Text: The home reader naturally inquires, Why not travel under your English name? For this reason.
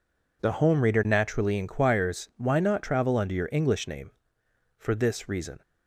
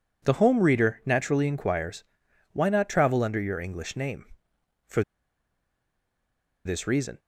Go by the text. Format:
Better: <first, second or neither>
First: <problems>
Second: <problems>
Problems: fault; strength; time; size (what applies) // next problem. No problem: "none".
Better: first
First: none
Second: pauses between "For" and "this"; strong; at 5.0 s; 1.6 s long